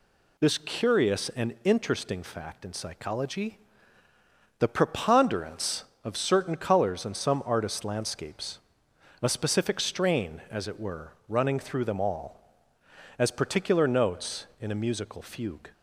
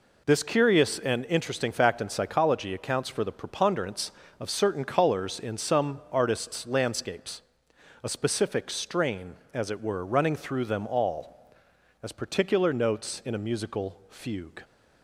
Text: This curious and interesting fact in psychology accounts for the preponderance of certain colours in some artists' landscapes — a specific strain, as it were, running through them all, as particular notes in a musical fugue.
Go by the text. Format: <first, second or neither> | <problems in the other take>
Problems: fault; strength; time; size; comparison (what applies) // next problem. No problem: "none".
second | skips "accounts for"; at 4.0 s